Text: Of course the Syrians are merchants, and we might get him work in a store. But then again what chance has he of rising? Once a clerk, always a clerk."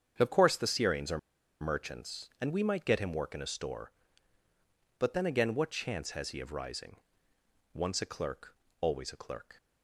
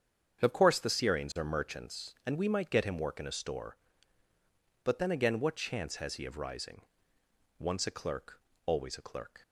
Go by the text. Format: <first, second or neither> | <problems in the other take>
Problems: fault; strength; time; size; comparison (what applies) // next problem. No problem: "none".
second | starts louder than the rest; strong; until 1.1 s; 7.5 dB; strong in the second // pauses between "are" and "merchants"; at 1.1 s; 0.42 s long